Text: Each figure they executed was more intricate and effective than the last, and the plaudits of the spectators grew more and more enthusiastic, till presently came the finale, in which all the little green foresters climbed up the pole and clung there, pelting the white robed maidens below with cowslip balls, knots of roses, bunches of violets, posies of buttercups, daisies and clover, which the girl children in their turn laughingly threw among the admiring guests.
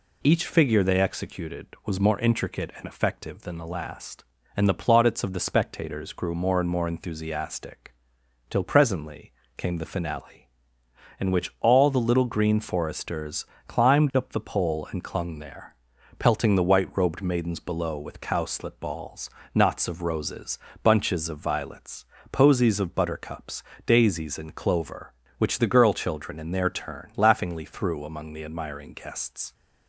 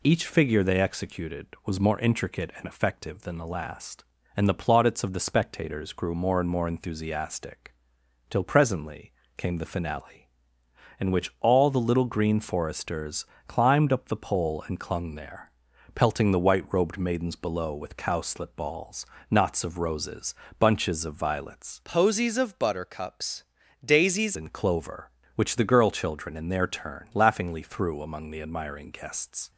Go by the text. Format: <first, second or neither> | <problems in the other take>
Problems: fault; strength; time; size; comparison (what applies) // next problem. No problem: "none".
first | pauses between "presently" and "came"; slight; at 9.1 s; 0.26 s long; slight in the first // pauses between "foresters" and "climbed"; slight; at 13.2 s; 0.20 s long; slight in the first // changes voice from "posies" to "daisies"; from 21.8 to 24.3 s; 2.5 s long